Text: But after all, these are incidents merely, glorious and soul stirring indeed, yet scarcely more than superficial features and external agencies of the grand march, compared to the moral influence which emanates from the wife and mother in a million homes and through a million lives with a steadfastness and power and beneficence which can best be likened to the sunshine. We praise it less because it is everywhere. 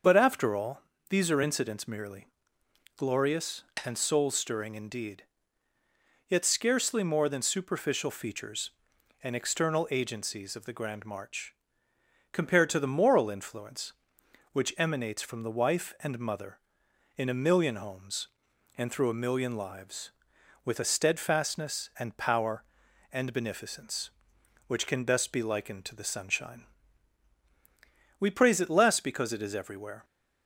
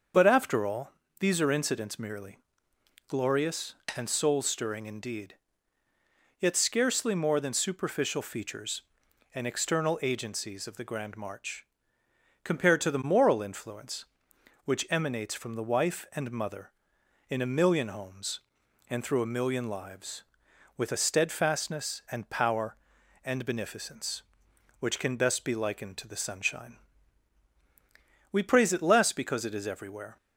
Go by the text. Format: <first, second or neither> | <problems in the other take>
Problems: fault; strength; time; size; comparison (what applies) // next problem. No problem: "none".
neither | starts louder than the rest; the same in both